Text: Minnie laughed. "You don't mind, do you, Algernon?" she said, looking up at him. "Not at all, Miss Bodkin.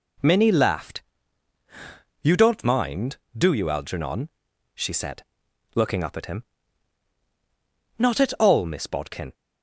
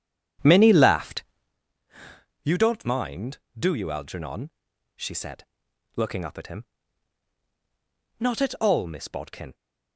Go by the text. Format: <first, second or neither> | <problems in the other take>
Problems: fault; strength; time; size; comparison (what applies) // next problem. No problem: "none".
first | starts louder than the rest; strong; until 1.6 s; 9 dB